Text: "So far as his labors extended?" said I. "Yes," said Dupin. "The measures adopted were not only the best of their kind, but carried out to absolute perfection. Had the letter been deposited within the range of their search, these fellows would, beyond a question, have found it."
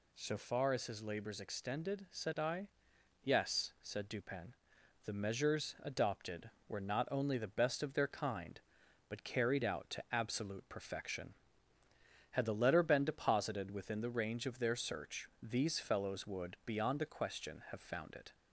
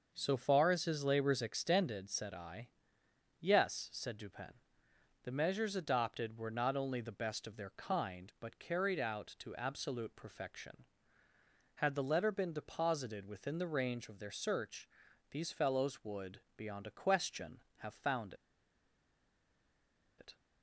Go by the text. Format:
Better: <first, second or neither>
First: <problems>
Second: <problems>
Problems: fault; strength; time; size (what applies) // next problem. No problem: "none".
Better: first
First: none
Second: starts louder than the rest; noticeable; until 1.1 s; 6 dB // pauses between "found" and "it"; strong; at 18.3 s; 1.8 s long